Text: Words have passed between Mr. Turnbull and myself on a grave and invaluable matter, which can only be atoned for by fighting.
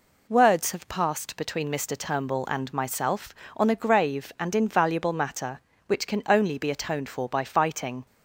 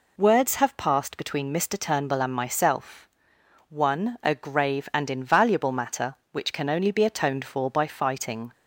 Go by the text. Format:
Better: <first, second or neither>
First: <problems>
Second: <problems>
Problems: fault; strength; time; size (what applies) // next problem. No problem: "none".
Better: first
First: none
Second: says "one" for "on"; at 3.6 s